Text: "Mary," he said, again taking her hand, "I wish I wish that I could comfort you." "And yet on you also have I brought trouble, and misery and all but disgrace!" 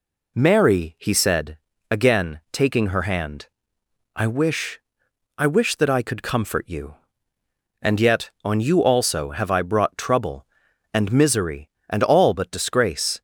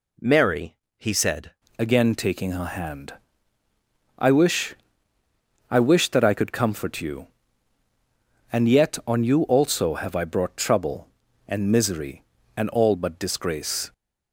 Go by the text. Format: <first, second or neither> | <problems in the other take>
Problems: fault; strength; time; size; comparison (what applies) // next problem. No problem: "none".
first | changes voice at "again"; from 1.7 s on; 12.2 s long // pauses between "wish" and "I"; noticeable; at 4.7 s; 0.96 s long; noticeable in the first